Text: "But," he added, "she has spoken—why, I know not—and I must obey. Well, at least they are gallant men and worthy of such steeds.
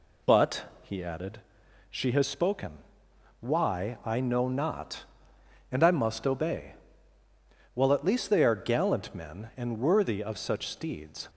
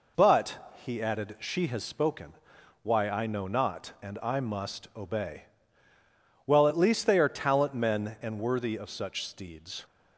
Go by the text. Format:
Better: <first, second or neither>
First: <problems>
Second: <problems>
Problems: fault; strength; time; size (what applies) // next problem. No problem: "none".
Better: first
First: none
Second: says "talent" for "gallant"; at 7.2 s